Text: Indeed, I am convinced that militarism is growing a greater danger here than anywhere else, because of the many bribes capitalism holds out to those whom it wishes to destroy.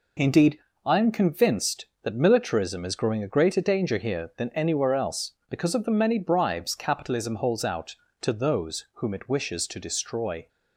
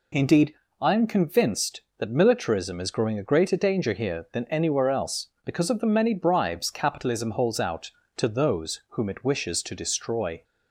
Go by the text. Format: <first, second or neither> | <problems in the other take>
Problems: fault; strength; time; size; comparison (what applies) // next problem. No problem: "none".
second | gets quieter; noticeable; throughout; 6 dB